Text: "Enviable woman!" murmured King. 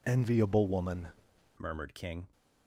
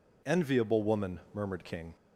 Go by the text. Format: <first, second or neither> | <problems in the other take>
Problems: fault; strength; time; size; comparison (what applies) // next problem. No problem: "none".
second | changes voice at "murmured"; from 1.5 s on; 0.7 s long